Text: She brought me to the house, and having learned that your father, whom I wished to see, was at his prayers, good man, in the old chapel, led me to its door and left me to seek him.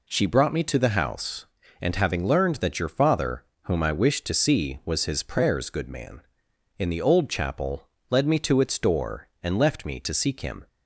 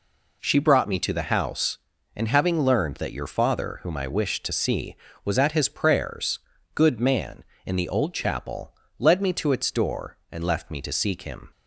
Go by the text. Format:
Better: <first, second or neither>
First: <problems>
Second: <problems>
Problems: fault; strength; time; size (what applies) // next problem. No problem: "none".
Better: second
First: skips "at"; at 5.0 s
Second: none